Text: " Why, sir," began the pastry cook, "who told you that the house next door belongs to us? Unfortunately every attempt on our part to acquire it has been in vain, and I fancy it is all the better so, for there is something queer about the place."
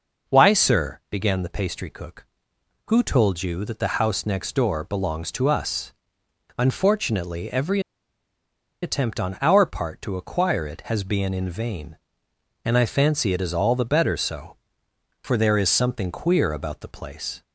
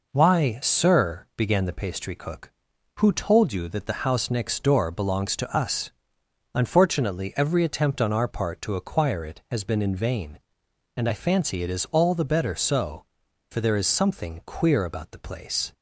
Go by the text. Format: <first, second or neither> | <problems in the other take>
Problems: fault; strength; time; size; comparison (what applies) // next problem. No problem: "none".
second | pauses between "every" and "attempt"; at 7.7 s; 1.0 s long